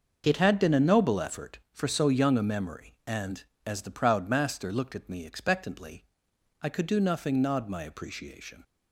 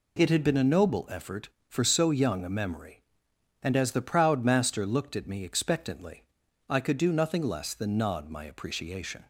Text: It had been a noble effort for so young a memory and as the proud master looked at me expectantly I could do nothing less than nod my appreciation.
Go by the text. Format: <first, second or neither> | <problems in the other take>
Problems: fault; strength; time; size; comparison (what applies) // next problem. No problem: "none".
second | starts louder than the rest; until 1.2 s; 6.5 dB // pauses between "expectantly" and "I"; noticeable; at 6.0 s; 0.60 s long; also in the second // skips "less than"; at 7.4 s